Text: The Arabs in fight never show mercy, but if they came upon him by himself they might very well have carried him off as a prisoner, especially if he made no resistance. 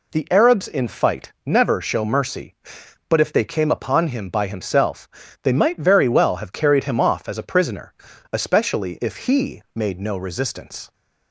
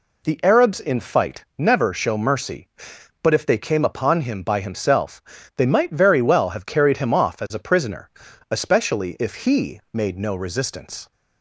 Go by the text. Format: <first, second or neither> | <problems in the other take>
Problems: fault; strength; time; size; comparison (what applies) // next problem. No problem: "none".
neither | pauses between "himself" and "they"; slight; the same in both